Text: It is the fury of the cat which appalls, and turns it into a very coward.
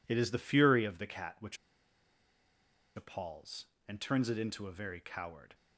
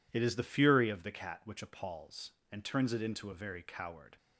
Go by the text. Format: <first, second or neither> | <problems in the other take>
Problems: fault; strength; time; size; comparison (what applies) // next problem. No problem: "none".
second | pauses between "which" and "appalls"; strong; at 1.5 s; 1.3 s long